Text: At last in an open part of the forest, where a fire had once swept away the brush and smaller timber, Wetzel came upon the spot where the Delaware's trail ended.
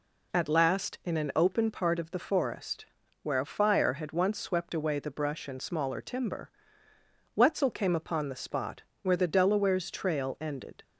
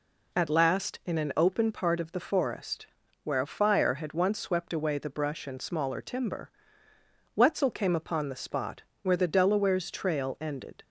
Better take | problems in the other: neither | pauses between "spot" and "where"; slight; the same in both

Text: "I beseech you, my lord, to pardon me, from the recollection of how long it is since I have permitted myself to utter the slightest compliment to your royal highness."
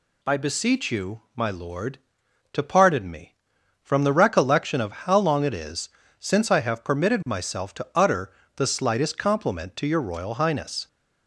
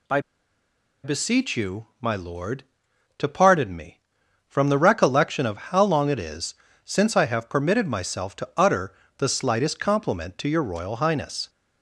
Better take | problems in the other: first | pauses between "I" and "beseech"; noticeable; at 0.1 s; 0.84 s long // pauses between "is" and "since"; slight; at 6.5 s; 0.30 s long; slight in the first // pauses between "utter" and "the"; slight; at 8.9 s; 0.24 s long; slight in the first

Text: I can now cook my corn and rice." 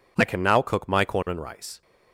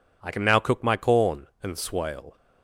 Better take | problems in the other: first | says "swale" for "rice"; at 1.7 s

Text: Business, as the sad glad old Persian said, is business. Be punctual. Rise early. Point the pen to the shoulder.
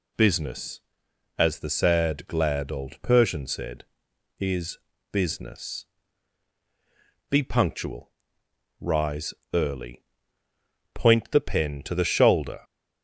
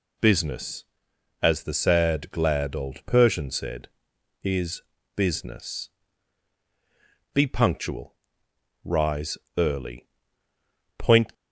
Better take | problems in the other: first | pauses between "is" and "business"; slight; at 4.8 s; 0.32 s long; slight in the first // pauses between "Rise" and "early"; slight; at 9.3 s; 0.20 s long; slight in the first // stops before "the pen to the shoulder"; at 11.3 s

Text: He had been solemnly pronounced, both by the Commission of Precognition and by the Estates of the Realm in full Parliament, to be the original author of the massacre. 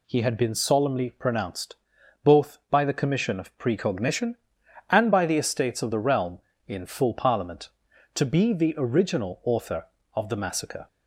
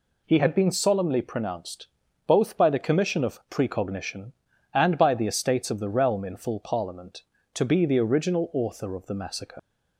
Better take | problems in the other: first | leaves "massacre" unfinished; at 9.5 s; 85 ms

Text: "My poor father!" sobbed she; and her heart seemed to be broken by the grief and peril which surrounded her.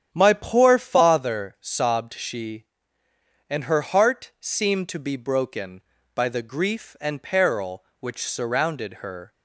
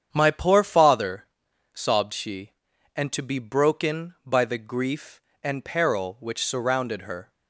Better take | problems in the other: first | starts louder than the rest; strong; until 1.1 s; 8.5 dB; strong in the first // skips "her heart seemed"; at 3.1 s

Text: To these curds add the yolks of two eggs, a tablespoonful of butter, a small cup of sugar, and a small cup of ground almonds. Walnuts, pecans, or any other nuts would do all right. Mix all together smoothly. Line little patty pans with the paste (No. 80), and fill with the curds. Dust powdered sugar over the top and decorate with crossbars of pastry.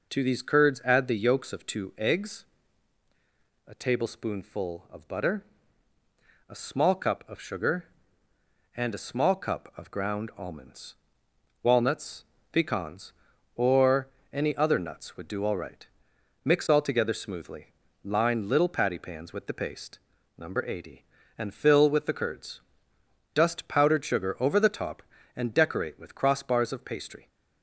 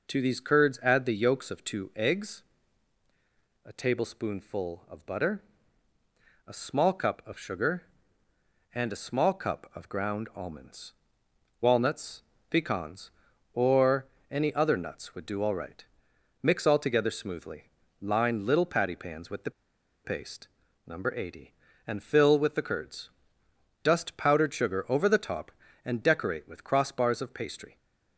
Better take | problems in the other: first | pauses between "or" and "any"; slight; at 14.0 s; 0.24 s long; slight in the first // pauses between "the" and "paste"; noticeable; at 19.5 s; 0.53 s long

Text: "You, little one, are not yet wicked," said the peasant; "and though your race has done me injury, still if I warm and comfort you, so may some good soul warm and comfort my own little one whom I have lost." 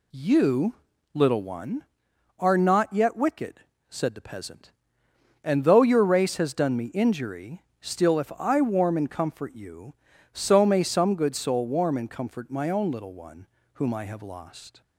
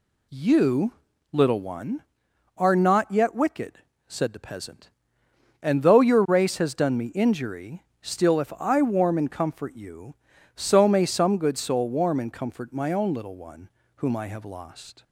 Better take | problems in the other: neither | pauses between "one" and "whom"; slight; the same in both

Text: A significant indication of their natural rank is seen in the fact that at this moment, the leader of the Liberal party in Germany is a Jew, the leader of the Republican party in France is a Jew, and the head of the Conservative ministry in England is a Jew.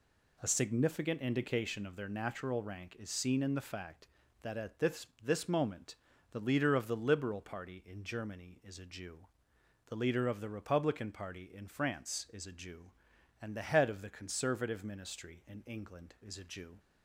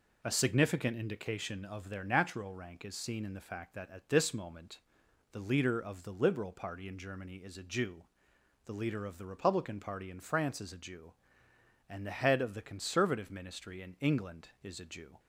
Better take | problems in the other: second | says "this" twice; at 5.2 s

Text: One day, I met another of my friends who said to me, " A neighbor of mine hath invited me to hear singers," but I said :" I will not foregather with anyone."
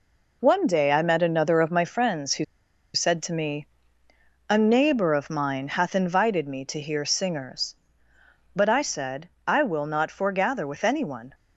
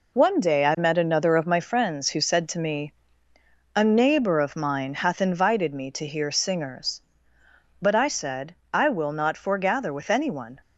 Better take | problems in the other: second | pauses between "who" and "said"; noticeable; at 2.4 s; 0.49 s long

